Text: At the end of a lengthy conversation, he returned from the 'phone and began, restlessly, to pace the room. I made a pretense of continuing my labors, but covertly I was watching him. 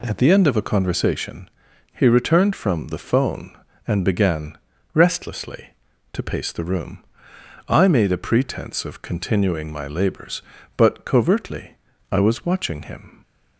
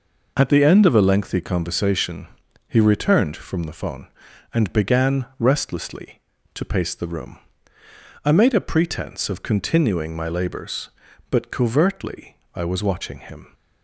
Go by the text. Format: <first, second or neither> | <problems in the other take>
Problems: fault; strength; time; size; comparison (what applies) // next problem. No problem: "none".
second | skips "lengthy"; at 0.6 s // pauses between "covertly" and "I"; slight; at 11.7 s; 0.34 s long; slight in the second